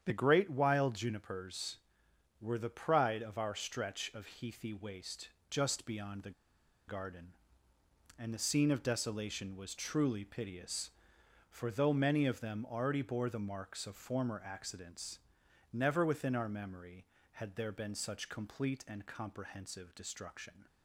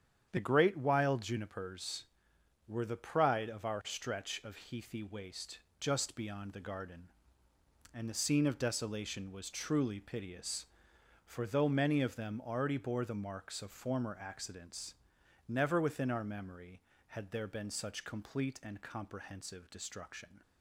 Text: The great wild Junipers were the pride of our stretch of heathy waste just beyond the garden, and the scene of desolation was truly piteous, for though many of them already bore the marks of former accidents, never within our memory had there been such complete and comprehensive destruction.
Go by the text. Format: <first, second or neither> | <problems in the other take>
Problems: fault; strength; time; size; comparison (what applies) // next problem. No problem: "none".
second | starts louder than the rest; strong; until 1.0 s; 8.5 dB; strong in the second // pauses between "waste" and "just"; slight; at 5.2 s; 0.24 s long; slight in the second // pauses between "the" and "garden"; noticeable; at 6.3 s; 0.56 s long